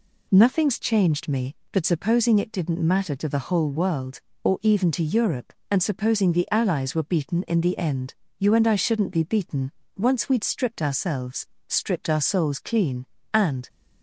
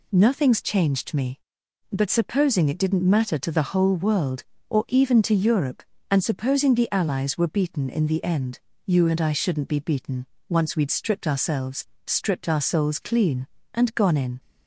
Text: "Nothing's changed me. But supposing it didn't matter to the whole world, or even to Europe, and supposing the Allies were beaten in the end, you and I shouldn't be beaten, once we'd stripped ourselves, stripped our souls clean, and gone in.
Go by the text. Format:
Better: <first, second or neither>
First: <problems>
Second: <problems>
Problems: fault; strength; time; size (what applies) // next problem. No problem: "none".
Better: second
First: stops before "gone in"; at 13.6 s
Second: none